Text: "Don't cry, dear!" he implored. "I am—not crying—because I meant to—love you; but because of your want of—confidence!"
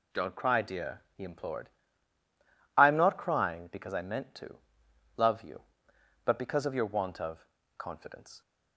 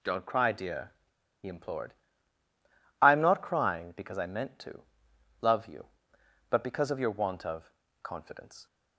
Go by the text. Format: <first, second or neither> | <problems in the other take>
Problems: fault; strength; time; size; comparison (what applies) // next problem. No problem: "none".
first | pauses between "he" and "implored"; slight; at 1.1 s; 0.35 s long